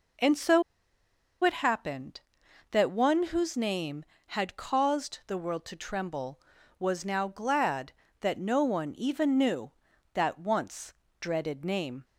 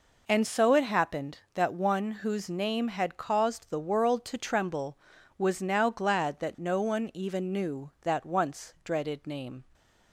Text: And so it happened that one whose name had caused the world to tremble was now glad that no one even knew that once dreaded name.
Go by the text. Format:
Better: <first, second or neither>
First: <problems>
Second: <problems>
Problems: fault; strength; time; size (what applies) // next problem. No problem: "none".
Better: second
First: pauses between "so" and "it"; noticeable; at 0.6 s; 0.80 s long // pauses between "once" and "dreaded"; slight; at 10.9 s; 0.26 s long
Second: none